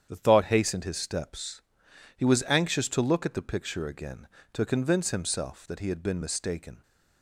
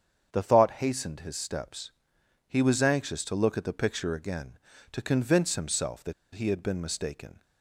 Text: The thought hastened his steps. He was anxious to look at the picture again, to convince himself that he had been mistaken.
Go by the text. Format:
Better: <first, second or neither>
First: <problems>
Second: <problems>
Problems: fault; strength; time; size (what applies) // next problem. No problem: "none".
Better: first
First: starts louder than the rest; strong; until 1.1 s; 8.5 dB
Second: starts louder than the rest; strong; until 1.3 s; 7.5 dB // pauses between "that" and "he"; slight; at 6.1 s; 0.21 s long